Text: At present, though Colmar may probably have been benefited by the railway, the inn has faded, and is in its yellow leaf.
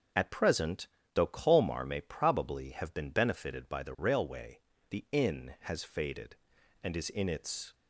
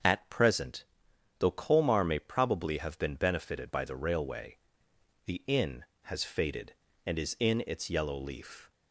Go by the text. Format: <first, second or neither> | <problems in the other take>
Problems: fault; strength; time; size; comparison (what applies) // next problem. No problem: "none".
second | starts louder than the rest; until 1.4 s; 6.5 dB; also in the second // stops before "yellow leaf"; at 7.7 s